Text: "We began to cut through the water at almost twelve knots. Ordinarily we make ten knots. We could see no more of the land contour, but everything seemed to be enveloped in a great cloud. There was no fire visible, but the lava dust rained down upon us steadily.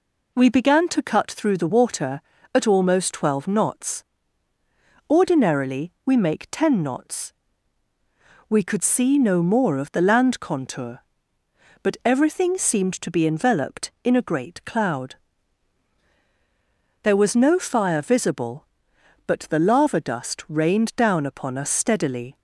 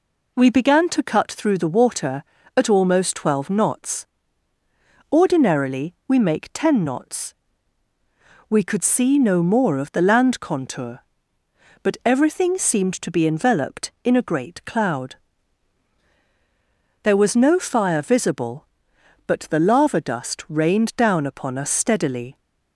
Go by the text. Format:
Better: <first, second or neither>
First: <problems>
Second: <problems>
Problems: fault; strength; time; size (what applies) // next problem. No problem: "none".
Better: neither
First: none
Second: none